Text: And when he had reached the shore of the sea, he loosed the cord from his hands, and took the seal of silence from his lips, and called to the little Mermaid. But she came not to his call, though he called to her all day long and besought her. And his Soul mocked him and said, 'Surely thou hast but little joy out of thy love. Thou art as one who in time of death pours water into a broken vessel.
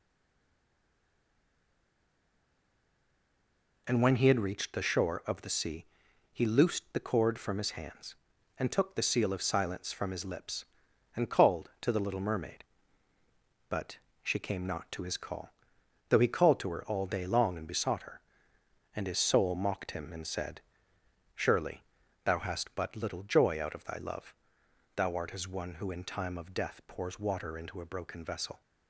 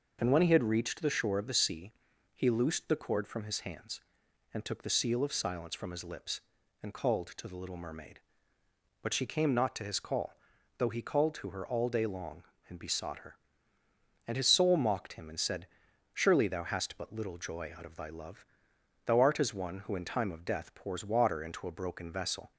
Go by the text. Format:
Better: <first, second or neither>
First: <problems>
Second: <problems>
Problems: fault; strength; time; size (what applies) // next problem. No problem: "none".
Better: second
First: stays silent before the first word; strong; until 3.8 s; 3.8 s long // pauses between "But" and "she"; slight; at 13.9 s; 0.24 s long // pauses between "Surely" and "thou"; at 21.8 s; 0.42 s long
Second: none